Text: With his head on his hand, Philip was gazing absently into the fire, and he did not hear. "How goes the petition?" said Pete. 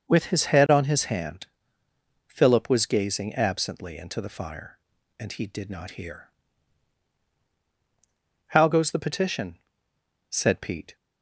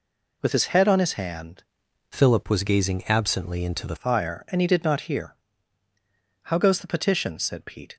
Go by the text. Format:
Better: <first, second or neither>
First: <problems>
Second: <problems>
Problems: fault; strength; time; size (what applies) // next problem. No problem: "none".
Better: first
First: none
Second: changes voice from "Philip" to "the"; from 2.0 to 3.9 s; 1.9 s long